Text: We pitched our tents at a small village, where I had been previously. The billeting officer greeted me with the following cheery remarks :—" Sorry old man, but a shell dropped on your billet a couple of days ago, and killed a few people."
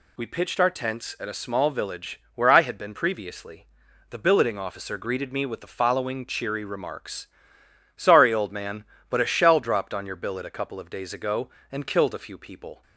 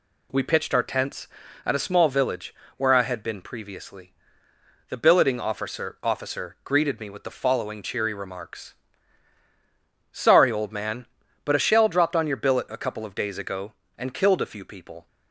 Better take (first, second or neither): first